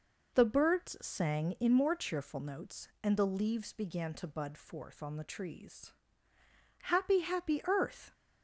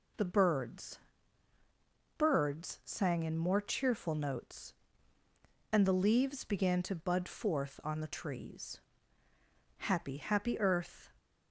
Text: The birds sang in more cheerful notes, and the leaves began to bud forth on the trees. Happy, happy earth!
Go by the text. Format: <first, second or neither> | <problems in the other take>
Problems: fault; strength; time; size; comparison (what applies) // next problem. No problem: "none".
first | says "birds" twice; at 2.1 s